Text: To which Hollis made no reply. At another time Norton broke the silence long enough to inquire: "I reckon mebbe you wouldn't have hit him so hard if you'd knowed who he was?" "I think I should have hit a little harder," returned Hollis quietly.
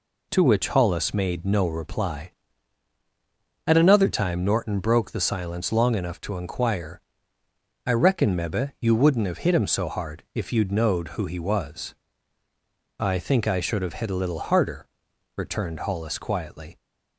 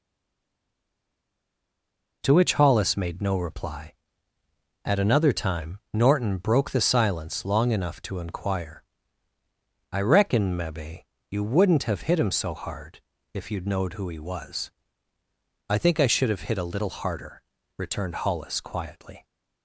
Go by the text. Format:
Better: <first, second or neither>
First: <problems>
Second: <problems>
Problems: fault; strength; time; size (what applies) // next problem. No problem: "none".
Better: first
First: none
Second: stays silent before the first word; until 2.2 s; 2.2 s long // pauses between "mebbe" and "you"; slight; at 11.0 s; 0.28 s long // pauses between "hard" and "if"; slight; at 12.9 s; 0.34 s long